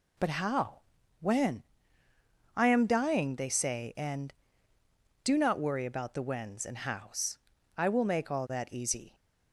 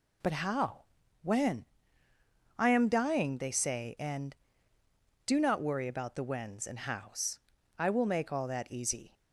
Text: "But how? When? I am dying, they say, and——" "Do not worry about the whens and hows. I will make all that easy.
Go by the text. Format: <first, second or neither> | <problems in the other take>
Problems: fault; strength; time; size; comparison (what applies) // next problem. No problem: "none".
neither | none